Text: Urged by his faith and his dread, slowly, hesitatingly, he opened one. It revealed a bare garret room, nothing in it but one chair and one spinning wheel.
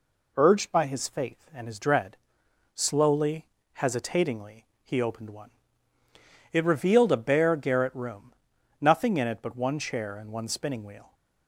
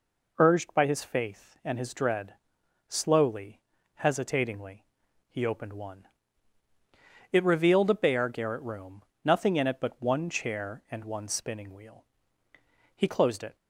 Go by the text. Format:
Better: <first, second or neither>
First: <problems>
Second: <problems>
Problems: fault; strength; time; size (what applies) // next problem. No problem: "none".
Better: first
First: none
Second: goes on to say "He closed it"; from 12.9 s on; 0.58 s long